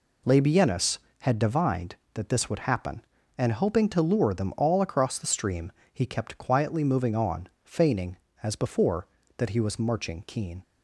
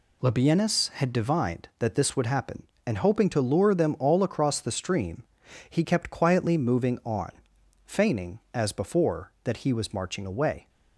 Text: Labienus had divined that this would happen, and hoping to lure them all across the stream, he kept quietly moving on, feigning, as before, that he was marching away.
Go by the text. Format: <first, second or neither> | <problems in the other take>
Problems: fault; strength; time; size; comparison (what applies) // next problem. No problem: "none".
second | says "keen" for "away"; at 10.2 s